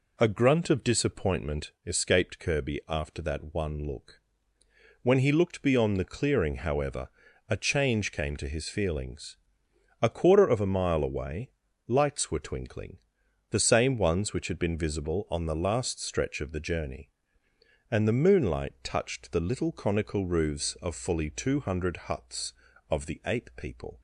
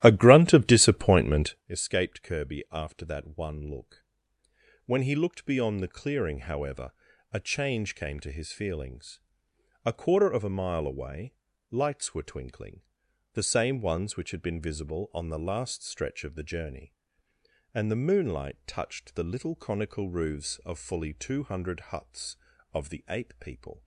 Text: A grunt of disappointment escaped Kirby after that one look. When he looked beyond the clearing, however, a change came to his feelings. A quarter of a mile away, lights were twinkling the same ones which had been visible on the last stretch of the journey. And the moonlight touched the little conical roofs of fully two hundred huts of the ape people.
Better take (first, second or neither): first